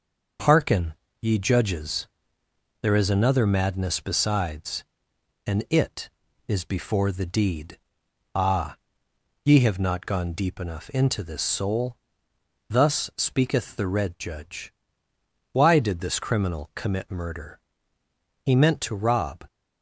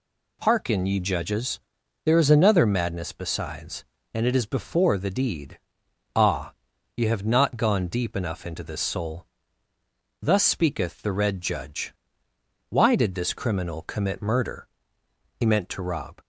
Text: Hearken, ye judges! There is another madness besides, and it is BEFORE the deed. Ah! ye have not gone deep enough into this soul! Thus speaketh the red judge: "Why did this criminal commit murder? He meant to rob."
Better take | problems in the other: neither | none

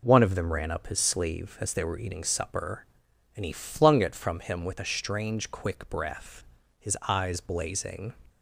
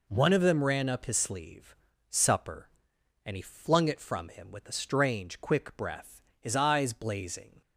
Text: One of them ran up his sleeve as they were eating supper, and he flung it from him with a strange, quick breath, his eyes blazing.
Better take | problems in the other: first | skips "as they were eating"; at 1.9 s

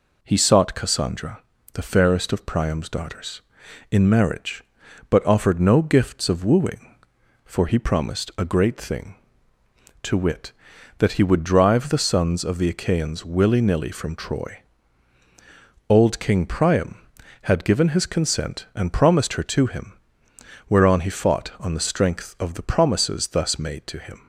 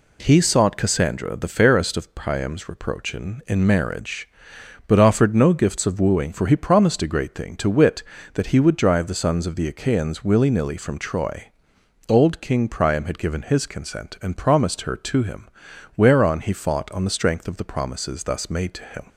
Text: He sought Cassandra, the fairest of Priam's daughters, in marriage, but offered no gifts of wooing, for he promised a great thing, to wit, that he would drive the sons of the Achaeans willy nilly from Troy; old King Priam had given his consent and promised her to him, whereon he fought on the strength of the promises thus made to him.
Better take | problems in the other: first | says "reproachin" for "daughters"; at 2.6 s

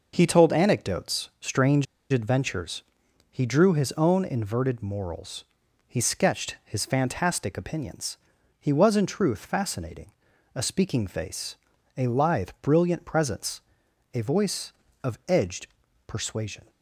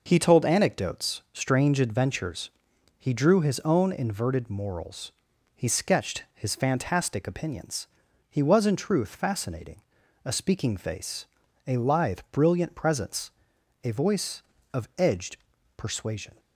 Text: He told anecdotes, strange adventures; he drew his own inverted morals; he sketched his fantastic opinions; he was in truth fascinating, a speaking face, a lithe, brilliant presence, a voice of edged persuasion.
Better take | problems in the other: second | pauses between "strange" and "adventures"; slight; at 1.8 s; 0.27 s long // pauses between "edged" and "persuasion"; at 15.6 s; 0.40 s long; also in the second

